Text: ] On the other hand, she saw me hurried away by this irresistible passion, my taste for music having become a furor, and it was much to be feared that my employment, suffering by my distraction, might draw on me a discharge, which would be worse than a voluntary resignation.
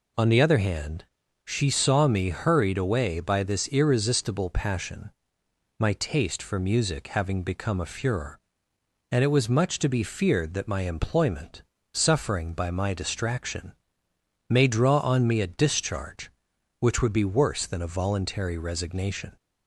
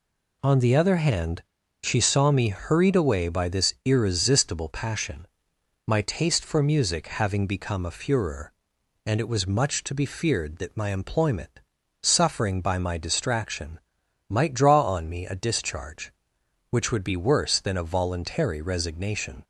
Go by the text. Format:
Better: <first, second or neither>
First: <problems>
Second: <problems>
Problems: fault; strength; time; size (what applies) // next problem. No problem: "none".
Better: second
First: says "may" for "might"; at 14.4 s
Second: none